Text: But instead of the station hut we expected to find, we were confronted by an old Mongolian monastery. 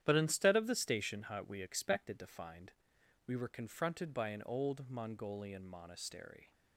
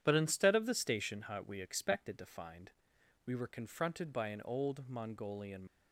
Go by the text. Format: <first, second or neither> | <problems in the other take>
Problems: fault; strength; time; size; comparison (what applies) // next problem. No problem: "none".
first | starts louder than the rest; strong; until 1.0 s; 9.5 dB; strong in the first // stops before "monastery"; at 5.6 s